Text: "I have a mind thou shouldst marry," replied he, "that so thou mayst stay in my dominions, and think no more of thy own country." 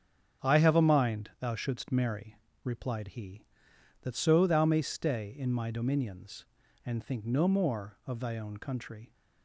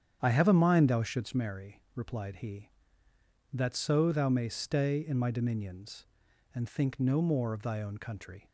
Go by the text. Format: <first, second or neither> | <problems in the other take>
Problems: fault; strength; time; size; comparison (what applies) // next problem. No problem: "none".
neither | starts louder than the rest; strong; the same in both